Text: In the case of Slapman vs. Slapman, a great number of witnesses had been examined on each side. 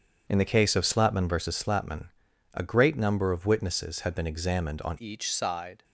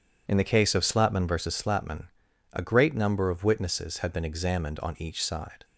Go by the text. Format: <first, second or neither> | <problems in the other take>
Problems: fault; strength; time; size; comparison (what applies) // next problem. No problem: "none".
second | starts louder than the rest; strong; until 1.2 s; 7 dB // changes voice at "each"; from 4.9 s on; 0.9 s long